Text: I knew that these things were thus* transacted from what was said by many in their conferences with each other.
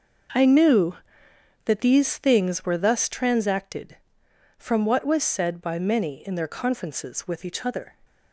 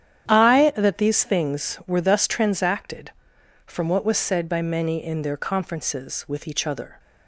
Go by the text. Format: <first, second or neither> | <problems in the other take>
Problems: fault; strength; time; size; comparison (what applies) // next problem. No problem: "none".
first | starts louder than the rest; strong; until 1.3 s; 9.5 dB; noticeable in the first // skips "knew"; at 0.7 s